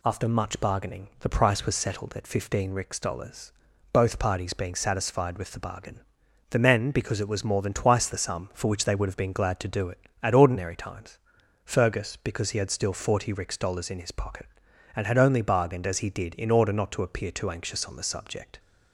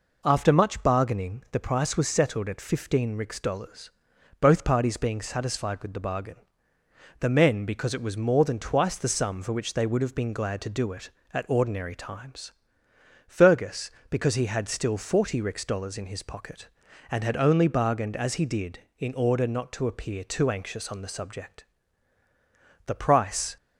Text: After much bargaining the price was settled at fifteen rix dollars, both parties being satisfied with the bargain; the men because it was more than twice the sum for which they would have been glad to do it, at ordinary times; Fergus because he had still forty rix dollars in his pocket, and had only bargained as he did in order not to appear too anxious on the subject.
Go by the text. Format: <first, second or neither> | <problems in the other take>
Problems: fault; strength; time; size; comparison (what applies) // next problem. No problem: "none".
first | goes on to say "The price"; noticeable; from 22.8 s on; 0.70 s long